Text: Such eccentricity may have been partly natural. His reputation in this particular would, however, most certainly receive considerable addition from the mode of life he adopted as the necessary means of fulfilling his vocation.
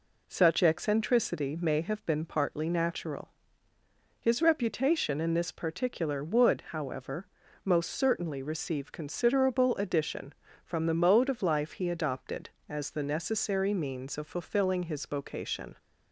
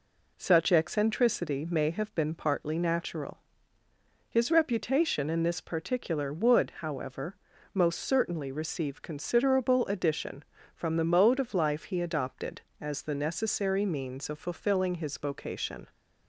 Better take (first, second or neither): neither